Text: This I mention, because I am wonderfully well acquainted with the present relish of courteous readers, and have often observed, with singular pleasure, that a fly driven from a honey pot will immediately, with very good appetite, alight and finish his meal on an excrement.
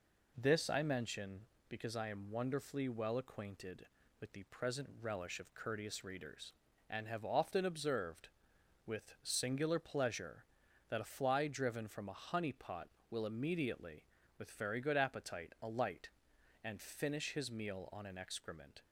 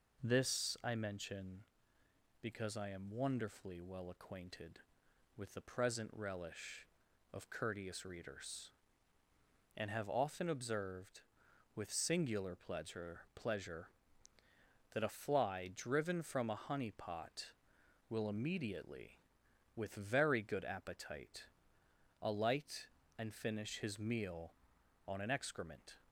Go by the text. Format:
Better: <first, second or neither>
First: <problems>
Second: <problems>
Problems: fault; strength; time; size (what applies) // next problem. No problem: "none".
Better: first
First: none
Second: says "pleasure" twice; at 13.3 s